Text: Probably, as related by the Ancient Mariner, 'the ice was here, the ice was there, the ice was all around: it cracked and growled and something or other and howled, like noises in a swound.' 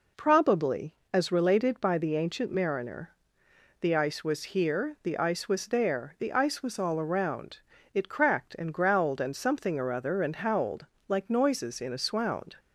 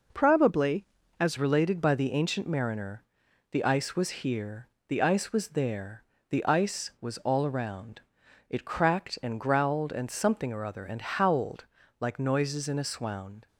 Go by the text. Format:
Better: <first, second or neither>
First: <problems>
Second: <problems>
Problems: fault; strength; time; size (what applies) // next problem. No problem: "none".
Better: first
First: none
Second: changes voice at "related"; from 1.3 s on; 12.1 s long